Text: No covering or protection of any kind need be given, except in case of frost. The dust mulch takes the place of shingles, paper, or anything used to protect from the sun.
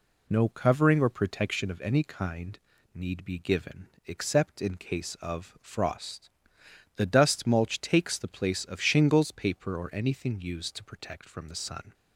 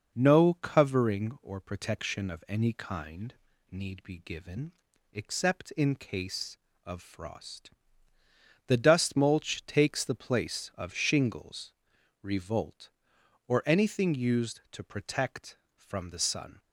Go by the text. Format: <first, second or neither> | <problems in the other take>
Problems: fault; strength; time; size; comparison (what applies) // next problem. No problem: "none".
first | pauses between "kind" and "need"; at 3.3 s; 0.38 s long; slight in the first // says "revolt" for "paper"; at 12.2 s